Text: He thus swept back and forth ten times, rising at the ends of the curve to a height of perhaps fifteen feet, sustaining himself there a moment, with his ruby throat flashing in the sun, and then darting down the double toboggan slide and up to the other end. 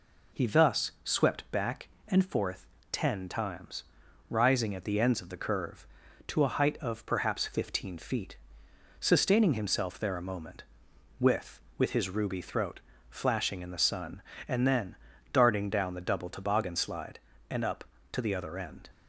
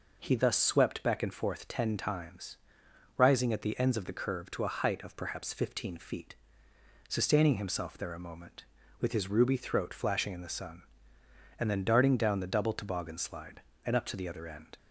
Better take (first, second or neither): second